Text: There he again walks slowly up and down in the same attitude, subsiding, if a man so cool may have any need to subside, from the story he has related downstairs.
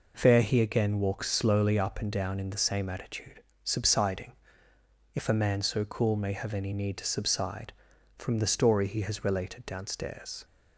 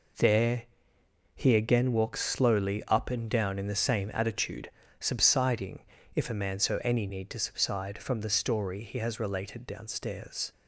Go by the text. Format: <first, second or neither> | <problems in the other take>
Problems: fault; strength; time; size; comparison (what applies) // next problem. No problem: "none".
first | pauses between "There" and "he"; noticeable; at 0.6 s; 0.68 s long // skips "cool may have"; at 6.8 s